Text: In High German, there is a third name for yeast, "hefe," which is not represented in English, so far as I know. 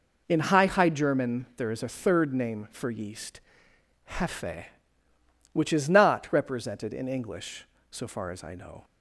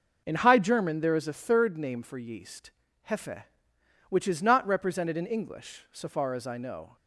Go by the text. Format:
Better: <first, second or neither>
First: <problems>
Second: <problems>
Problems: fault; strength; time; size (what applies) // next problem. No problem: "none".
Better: second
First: says "High" twice; at 0.6 s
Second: none